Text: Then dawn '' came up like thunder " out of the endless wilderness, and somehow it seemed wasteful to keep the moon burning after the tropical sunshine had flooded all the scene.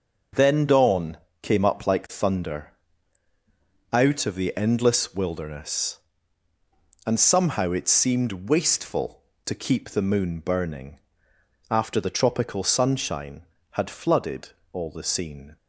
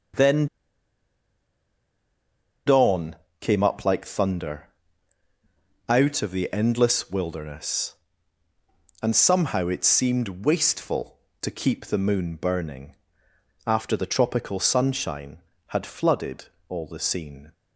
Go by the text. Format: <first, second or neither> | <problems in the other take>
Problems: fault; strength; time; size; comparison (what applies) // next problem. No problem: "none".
first | pauses between "Then" and "dawn"; strong; at 0.4 s; 2.1 s long // pauses between "burning" and "after"; noticeable; at 12.9 s; 0.72 s long; noticeable in the first // pauses between "flooded" and "all"; slight; at 16.4 s; 0.22 s long; slight in the first